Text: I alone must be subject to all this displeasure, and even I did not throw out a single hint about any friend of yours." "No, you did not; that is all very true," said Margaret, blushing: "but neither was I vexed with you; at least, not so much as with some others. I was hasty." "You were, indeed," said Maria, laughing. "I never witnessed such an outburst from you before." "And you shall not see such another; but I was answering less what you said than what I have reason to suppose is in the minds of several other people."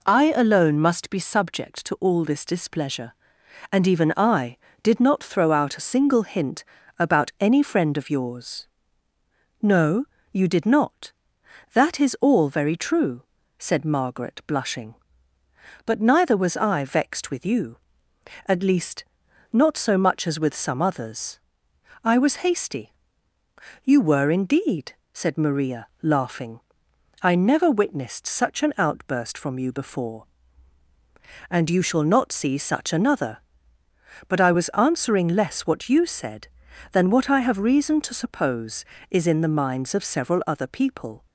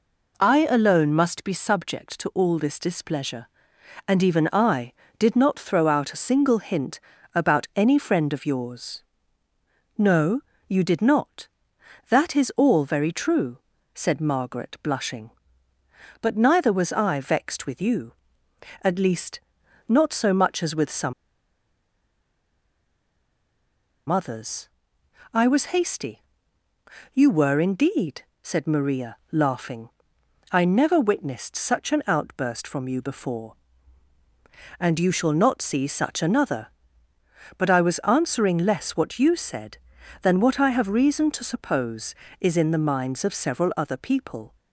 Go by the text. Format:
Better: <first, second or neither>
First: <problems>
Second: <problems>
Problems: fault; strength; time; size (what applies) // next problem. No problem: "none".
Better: first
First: pauses between "hint" and "about"; slight; at 6.6 s; 0.34 s long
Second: pauses between "hint" and "about"; slight; at 6.9 s; 0.34 s long // pauses between "some" and "others"; strong; at 21.1 s; 2.9 s long